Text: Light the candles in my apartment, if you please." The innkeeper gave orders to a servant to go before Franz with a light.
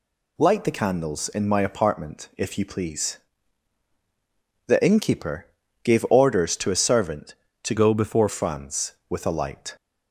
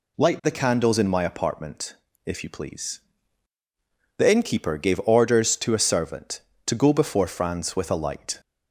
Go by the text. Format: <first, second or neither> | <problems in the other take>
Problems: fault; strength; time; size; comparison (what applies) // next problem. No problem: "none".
second | pauses between "innkeeper" and "gave"; slight; at 5.4 s; 0.36 s long // changes voice from "go" to "before"; from 7.7 to 8.2 s; 0.5 s long